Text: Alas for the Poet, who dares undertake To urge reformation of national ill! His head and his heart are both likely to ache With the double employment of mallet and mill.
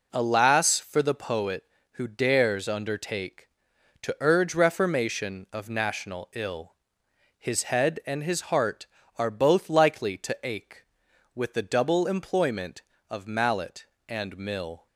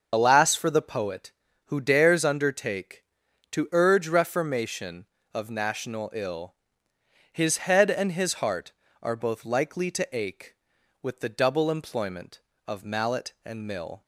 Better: first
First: none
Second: loses the start of "Alas"; at 0.1 s; 30 ms // starts louder than the rest; until 1.1 s; 6.5 dB

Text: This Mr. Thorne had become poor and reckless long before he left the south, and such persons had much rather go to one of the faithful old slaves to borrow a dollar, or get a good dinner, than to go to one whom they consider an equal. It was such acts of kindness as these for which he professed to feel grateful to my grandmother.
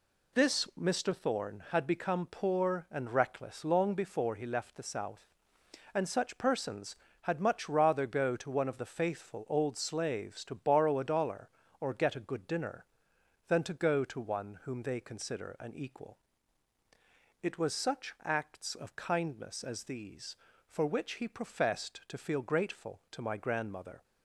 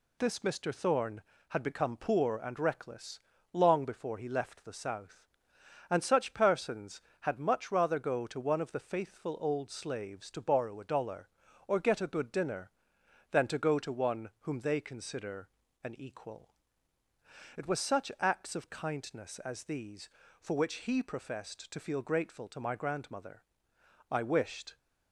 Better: first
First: none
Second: pauses between "reckless" and "long"; slight; at 3.1 s; 0.34 s long // pauses between "consider" and "an"; slight; at 15.4 s; 0.36 s long // goes on to say "I wished"; noticeable; from 24.0 s on; 0.68 s long

